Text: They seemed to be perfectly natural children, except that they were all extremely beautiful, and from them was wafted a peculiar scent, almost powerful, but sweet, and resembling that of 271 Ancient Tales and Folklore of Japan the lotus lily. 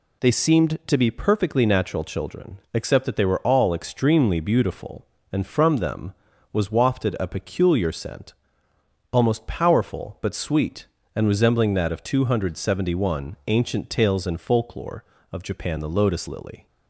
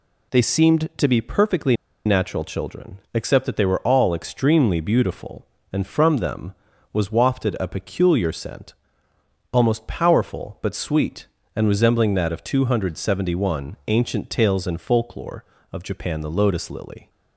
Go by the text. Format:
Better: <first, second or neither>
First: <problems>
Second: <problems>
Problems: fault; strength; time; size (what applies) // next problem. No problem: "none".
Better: first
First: none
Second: pauses between "perfectly" and "natural"; slight; at 1.7 s; 0.30 s long